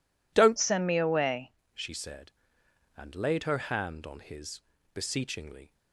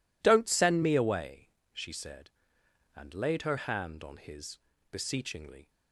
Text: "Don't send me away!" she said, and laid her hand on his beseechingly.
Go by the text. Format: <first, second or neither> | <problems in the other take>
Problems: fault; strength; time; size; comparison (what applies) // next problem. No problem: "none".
second | changes voice from "send" to "away"; from 0.5 to 1.5 s; 1.0 s long // pauses between "his" and "beseechingly"; slight; at 4.5 s; 0.34 s long; slight in the second